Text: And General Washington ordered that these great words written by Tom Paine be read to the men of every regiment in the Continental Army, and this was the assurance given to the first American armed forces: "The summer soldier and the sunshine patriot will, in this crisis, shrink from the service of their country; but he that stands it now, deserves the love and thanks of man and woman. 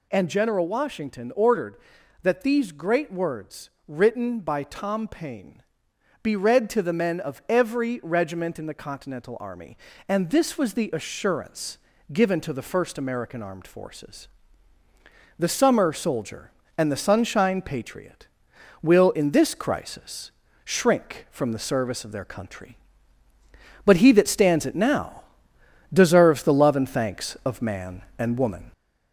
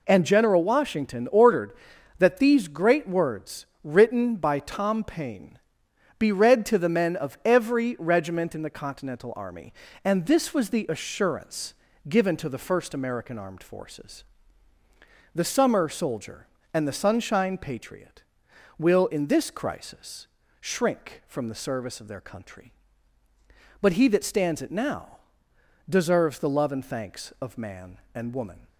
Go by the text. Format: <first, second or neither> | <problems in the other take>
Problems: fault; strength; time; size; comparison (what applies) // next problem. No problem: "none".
second | gets louder; slight; throughout; 2.5 dB // pauses between "words" and "written"; slight; at 3.6 s; 0.16 s long; slight in the second // pauses between "Paine" and "be"; noticeable; at 5.6 s; 0.60 s long; noticeable in the second // pauses between "assurance" and "given"; slight; at 11.7 s; 0.34 s long; slight in the second